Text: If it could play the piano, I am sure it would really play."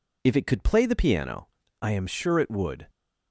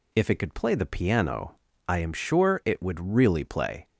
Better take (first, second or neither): second